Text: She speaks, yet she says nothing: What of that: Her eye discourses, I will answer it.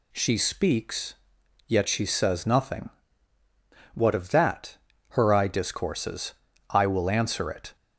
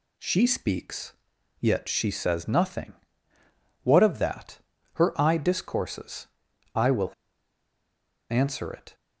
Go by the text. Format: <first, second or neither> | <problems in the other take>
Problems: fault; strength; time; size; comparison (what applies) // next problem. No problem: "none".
first | pauses between "will" and "answer"; at 7.1 s; 1.1 s long